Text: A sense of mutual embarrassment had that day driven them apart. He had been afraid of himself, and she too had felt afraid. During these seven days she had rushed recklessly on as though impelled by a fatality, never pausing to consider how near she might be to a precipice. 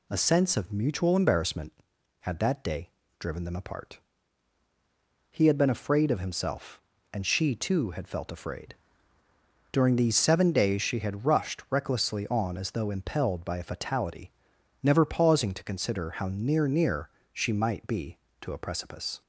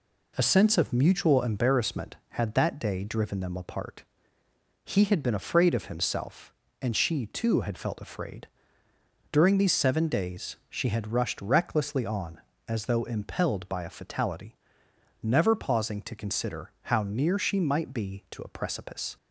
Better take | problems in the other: second | pauses between "day" and "driven"; slight; at 2.8 s; 0.30 s long // says "near" twice; at 16.6 s

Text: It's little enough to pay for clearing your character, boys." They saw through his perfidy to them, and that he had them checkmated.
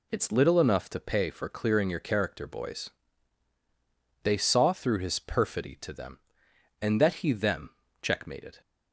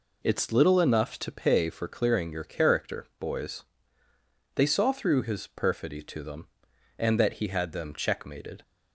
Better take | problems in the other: second | skips "had"; at 7.3 s // pauses between "them" and "checkmated"; slight; at 7.6 s; 0.32 s long

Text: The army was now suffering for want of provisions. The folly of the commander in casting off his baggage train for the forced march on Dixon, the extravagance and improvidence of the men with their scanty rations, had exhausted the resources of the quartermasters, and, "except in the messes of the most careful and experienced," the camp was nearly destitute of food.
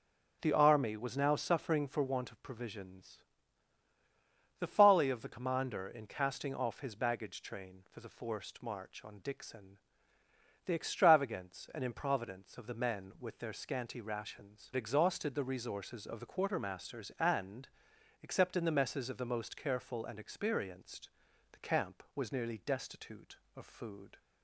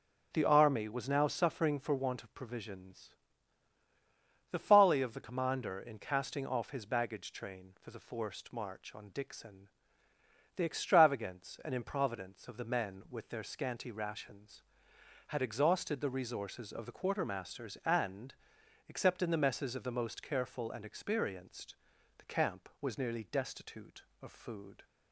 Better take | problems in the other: second | starts louder than the rest; noticeable; until 1.4 s; 6 dB; noticeable in the second // skips "had"; at 14.7 s

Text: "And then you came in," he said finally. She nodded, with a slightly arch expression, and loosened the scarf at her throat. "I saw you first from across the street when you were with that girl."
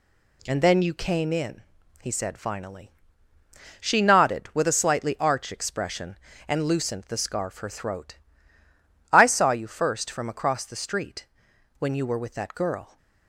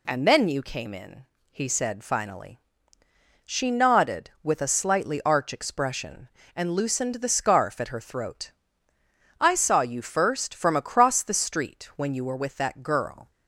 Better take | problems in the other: second | skips "at"; at 7.5 s // pauses between "street" and "when"; noticeable; at 11.2 s; 0.52 s long

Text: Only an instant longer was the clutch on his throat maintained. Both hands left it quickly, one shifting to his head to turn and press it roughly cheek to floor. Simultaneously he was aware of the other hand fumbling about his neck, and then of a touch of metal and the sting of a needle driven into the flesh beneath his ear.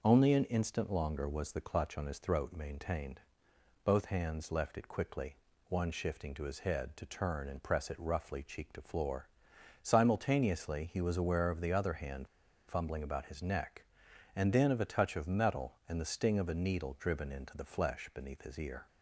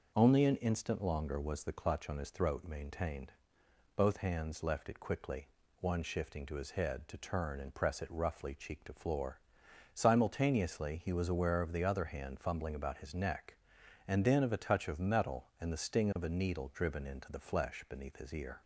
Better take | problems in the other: second | pauses between "hand" and "fumbling"; at 12.2 s; 0.40 s long

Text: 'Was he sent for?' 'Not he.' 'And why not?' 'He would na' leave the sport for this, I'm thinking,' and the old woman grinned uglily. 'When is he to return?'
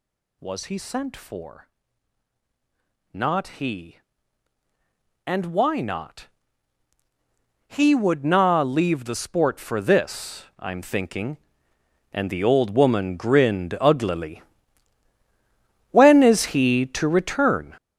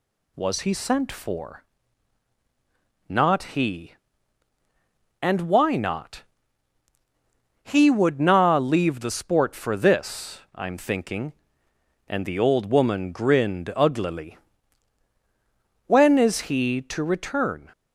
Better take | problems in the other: second | gets louder; strong; throughout; 11.5 dB

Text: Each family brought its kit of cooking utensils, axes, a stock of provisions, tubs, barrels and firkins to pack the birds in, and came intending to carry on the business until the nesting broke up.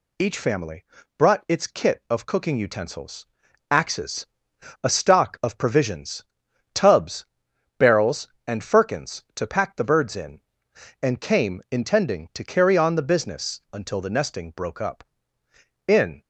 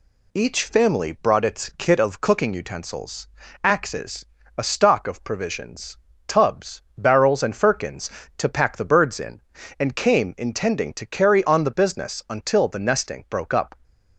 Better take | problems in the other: second | pauses between "family" and "brought"; slight; at 0.8 s; 0.32 s long // goes on to say "In"; slight; from 15.8 s on; 0.38 s long

